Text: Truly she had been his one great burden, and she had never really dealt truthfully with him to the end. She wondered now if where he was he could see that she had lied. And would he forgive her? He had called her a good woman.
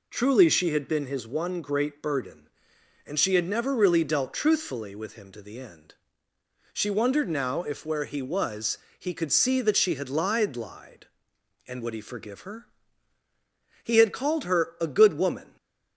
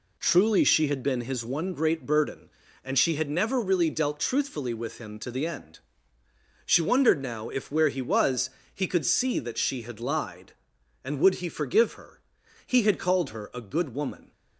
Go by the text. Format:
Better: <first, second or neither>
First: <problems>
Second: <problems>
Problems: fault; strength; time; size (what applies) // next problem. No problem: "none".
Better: second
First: pauses between "was" and "he"; slight; at 8.7 s; 0.20 s long // says "lied" twice; at 10.5 s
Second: pauses between "was" and "he"; slight; at 8.4 s; 0.24 s long